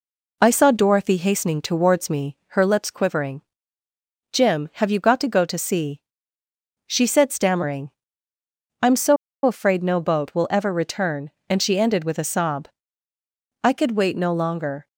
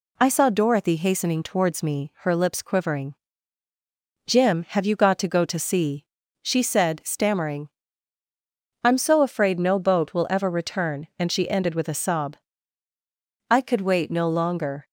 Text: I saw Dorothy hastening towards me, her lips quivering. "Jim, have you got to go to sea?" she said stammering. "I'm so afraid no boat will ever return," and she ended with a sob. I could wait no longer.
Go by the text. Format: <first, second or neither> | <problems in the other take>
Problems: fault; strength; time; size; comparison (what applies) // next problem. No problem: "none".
second | pauses between "so" and "afraid"; slight; at 9.1 s; 0.28 s long